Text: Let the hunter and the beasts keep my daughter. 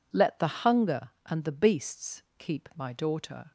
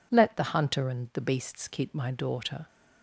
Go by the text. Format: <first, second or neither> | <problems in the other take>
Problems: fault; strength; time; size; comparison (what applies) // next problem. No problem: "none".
second | says "hunger" for "hunter"; at 0.6 s // pauses between "beasts" and "keep"; slight; at 2.2 s; 0.16 s long